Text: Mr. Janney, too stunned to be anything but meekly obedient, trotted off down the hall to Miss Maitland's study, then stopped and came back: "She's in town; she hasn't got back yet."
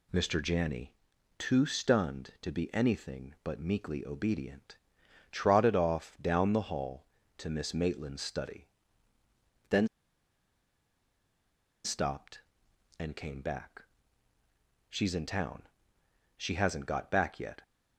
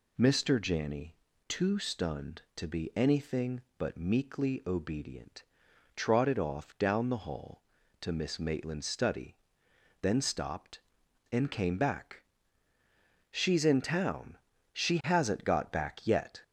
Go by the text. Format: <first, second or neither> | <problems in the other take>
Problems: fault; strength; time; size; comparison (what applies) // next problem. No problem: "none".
second | pauses between "then" and "stopped"; strong; at 9.8 s; 1.9 s long